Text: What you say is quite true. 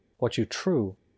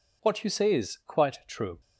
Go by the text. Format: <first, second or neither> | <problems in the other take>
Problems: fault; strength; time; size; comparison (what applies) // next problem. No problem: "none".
second | skips "say is quite"; at 0.4 s